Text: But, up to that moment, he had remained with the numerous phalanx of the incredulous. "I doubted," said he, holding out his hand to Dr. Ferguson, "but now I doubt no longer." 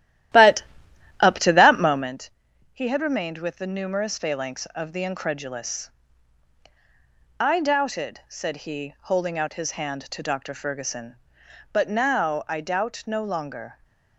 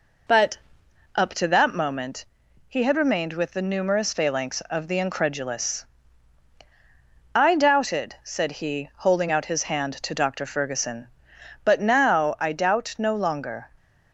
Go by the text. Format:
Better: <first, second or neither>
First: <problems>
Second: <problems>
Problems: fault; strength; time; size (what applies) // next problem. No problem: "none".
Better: second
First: starts louder than the rest; strong; until 2.2 s; 13 dB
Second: none